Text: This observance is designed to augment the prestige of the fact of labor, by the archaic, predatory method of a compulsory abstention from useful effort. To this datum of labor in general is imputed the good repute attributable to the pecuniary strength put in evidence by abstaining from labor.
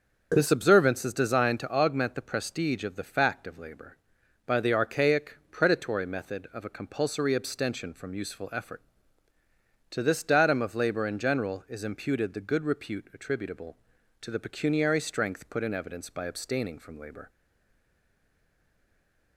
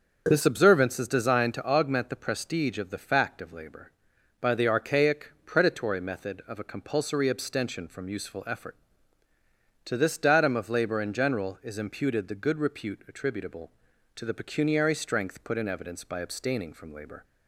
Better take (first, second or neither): second